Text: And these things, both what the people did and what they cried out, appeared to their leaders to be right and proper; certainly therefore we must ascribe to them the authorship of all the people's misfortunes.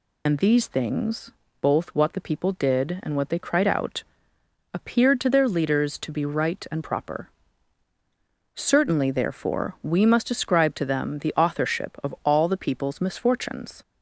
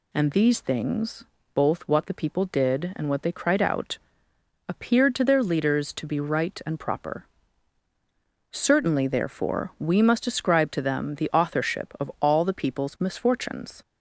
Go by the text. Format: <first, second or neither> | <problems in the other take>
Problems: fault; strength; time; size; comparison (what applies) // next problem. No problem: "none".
second | loses the start of "And"; at 0.2 s; 45 ms